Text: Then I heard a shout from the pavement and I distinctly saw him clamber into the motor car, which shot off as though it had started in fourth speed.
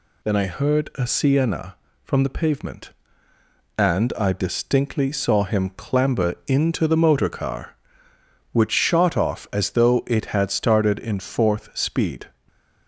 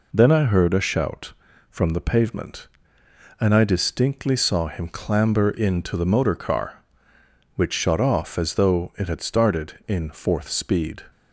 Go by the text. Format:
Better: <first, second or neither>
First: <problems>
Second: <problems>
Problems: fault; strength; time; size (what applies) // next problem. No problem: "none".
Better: second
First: says "sienna" for "shout"; at 1.0 s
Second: none